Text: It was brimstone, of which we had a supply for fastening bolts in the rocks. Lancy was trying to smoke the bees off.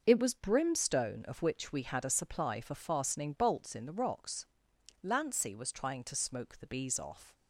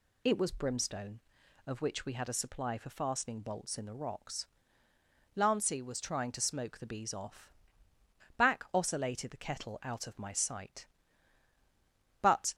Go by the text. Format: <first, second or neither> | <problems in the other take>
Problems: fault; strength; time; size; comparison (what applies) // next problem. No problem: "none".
first | goes on to say "Back oscillated the kettle out of my sight But"; strong; from 8.3 s on; 4.1 s long